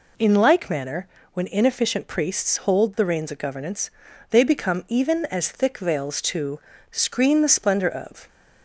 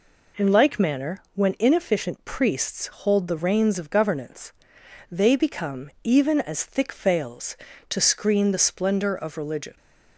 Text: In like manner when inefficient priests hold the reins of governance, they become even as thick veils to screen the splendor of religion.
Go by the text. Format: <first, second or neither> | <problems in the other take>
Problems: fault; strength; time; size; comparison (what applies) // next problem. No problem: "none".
second | pauses between "manner" and "when"; slight; at 1.0 s; 0.26 s long // pauses between "to" and "screen"; slight; at 6.5 s; 0.30 s long // stops before "religion"; at 8.2 s